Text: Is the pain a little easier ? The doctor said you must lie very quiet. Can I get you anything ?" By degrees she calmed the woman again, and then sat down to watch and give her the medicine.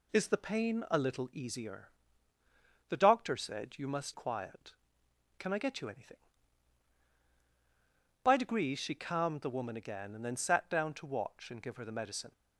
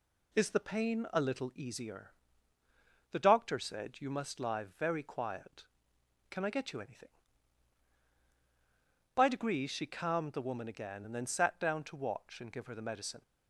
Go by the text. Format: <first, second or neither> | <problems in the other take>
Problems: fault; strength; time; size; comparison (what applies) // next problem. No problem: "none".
second | skips "lie very"; at 4.1 s